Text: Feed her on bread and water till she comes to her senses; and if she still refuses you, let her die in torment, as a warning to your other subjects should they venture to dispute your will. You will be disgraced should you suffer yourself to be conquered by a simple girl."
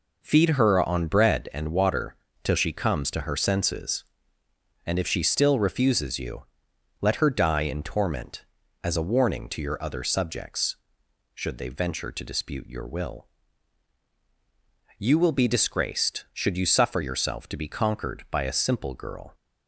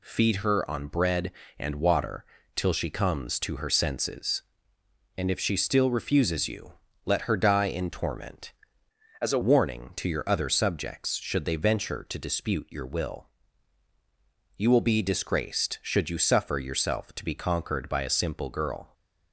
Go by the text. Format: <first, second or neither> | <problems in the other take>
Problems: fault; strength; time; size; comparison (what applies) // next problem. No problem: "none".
first | pauses between "water" and "till"; slight; at 2.2 s; 0.30 s long; slight in the first // changes voice from "as" to "a"; from 9.2 to 9.3 s; 0.1 s long